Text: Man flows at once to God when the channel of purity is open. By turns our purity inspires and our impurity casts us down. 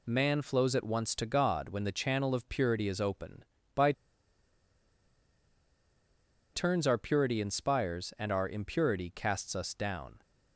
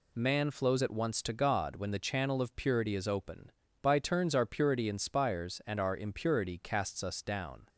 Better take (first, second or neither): second